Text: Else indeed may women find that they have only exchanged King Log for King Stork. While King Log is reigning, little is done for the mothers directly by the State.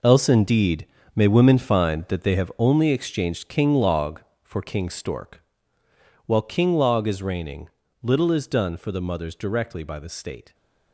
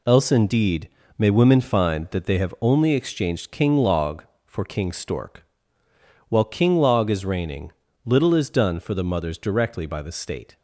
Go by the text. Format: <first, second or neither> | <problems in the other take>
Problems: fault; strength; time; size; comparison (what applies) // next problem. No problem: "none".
second | gets quieter; strong; throughout; 11.5 dB // pauses between "indeed" and "may"; slight; at 0.8 s; 0.28 s long; slight in the second